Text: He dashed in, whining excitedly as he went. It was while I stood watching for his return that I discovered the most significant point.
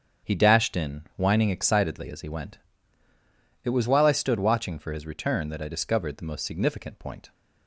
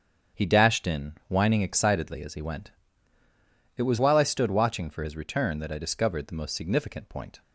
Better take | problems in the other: neither | starts louder than the rest; strong; the same in both

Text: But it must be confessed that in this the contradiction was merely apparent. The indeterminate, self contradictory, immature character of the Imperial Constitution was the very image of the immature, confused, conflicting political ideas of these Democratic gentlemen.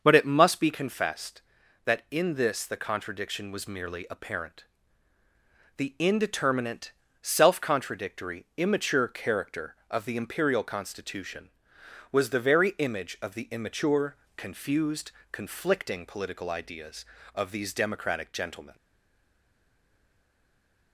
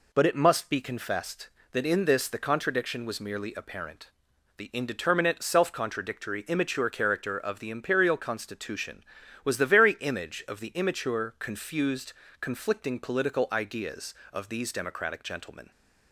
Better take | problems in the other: second | starts louder than the rest; until 1.0 s; 6.5 dB // stays silent after the last word; from 18.7 s on; 2.2 s long

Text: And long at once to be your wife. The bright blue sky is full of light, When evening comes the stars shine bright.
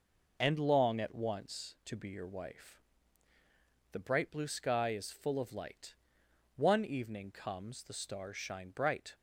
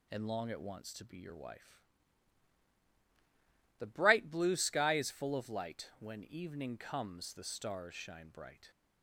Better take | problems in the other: second | says "One" for "When"; at 6.5 s

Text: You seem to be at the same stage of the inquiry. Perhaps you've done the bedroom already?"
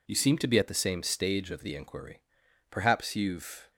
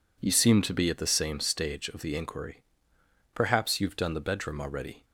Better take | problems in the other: second | stops before "done the bedroom already"; at 3.7 s

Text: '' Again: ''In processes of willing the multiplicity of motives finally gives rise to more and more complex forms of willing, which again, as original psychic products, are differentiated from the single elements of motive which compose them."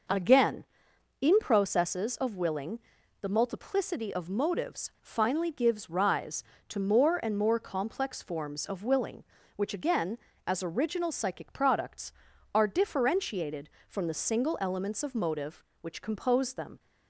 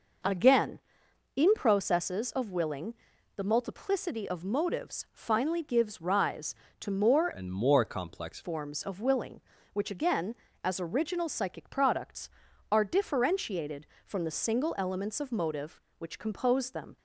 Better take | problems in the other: first | pauses between "willing" and "the"; at 2.9 s; 0.40 s long; also in the first // changes voice from "and" to "complex"; from 7.3 to 8.4 s; 1.1 s long

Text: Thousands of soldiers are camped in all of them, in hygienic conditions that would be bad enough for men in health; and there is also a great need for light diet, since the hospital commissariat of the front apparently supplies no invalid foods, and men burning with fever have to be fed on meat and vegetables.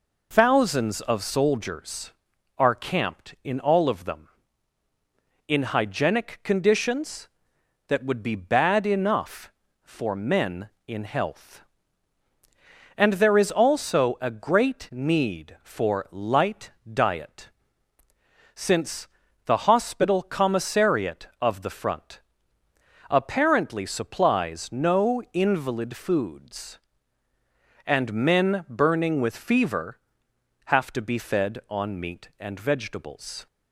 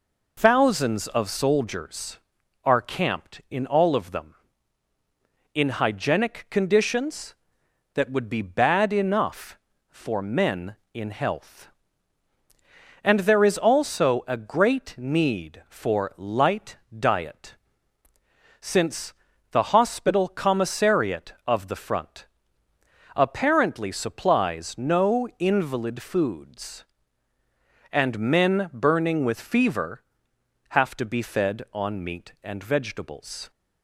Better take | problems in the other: neither | pauses between "light" and "diet"; slight; the same in both // pauses between "since" and "the"; slight; the same in both // pauses between "front" and "apparently"; noticeable; the same in both

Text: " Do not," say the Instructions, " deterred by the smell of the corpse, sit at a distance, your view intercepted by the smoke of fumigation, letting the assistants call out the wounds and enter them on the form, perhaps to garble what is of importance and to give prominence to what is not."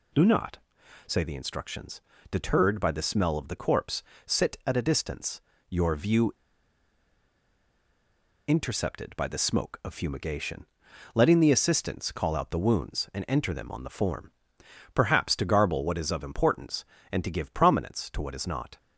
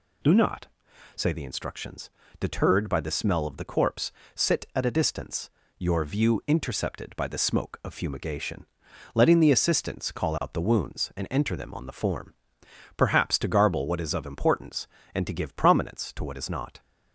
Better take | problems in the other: second | pauses between "view" and "intercepted"; strong; at 6.3 s; 2.1 s long

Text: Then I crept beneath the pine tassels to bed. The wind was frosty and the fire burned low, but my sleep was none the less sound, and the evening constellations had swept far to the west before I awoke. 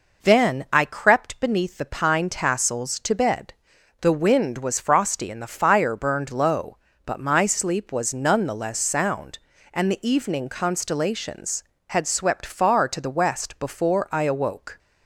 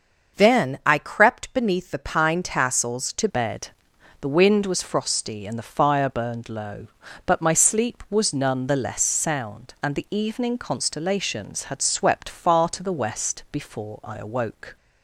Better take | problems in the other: first | starts louder than the rest; noticeable; until 1.4 s; 6 dB // changes voice at "bed"; from 3.2 s on; 11.5 s long

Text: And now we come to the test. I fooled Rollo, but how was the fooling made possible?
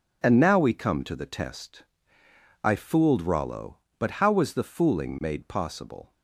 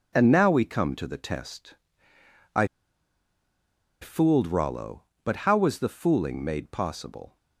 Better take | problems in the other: first | pauses between "I" and "fooled"; strong; at 2.6 s; 1.3 s long

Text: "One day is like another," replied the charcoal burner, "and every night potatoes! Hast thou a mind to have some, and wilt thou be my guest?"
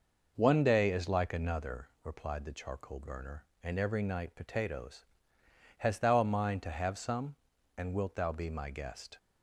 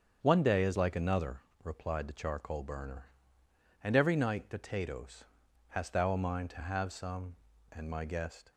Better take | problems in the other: first | starts louder than the rest; strong; until 1.2 s; 7.5 dB // skips "wilt thou be"; at 7.8 s

